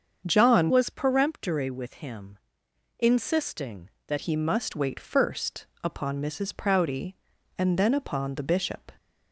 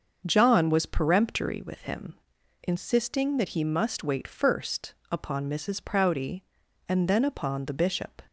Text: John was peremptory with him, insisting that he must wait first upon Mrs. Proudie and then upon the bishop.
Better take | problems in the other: second | starts louder than the rest; until 1.2 s; 7 dB; also in the second // changes voice from "was" to "that"; from 0.6 to 4.1 s; 3.5 s long // pauses between "first" and "upon"; slight; at 5.6 s; 0.18 s long; slight in the second

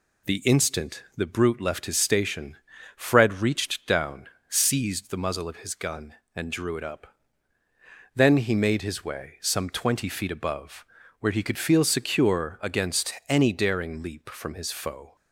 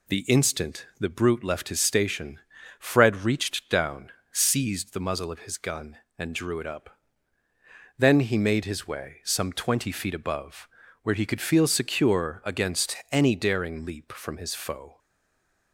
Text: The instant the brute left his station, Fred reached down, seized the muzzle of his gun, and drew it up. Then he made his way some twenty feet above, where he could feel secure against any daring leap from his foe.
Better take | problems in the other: first | stays silent after the last word; slight; from 14.9 s on; 0.8 s long

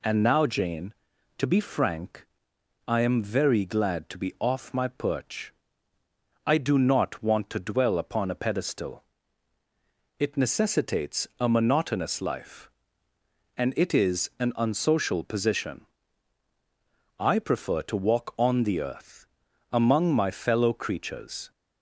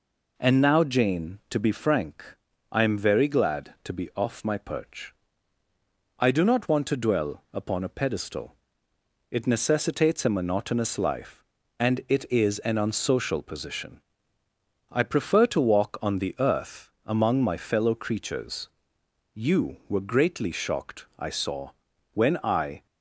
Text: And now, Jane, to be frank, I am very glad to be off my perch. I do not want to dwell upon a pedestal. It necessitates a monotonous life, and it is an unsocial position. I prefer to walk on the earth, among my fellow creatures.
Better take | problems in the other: first | goes on to say "You were greatly shocked I saw when I"; strong; from 19.3 s on; 3.5 s long

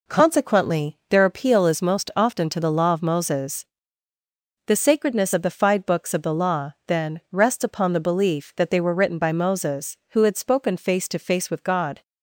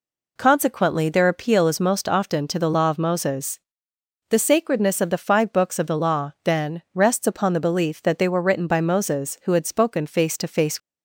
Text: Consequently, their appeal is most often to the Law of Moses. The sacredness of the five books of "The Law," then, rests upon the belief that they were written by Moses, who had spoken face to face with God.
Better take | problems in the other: first | stops before "with God"; at 10.7 s

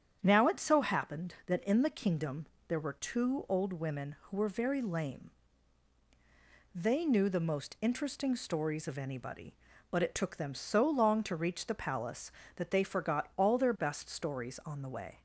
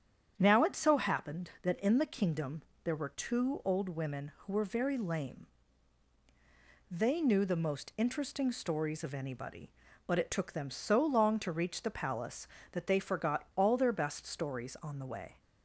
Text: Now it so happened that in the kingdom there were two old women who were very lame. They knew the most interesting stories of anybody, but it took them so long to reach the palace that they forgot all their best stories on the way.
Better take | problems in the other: neither | starts louder than the rest; strong; the same in both // pauses between "kingdom" and "there"; slight; the same in both

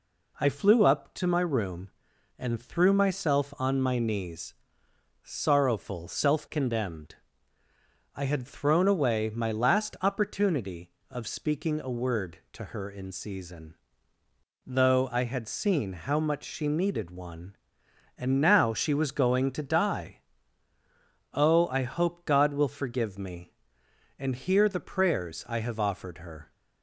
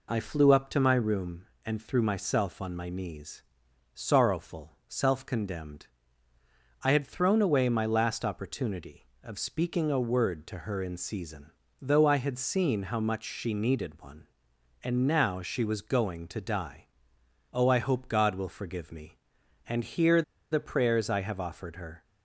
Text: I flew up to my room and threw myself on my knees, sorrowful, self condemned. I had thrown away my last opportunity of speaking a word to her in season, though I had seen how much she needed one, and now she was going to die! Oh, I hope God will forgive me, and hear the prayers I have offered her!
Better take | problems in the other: first | pauses between "hear" and "the"; slight; at 20.2 s; 0.28 s long

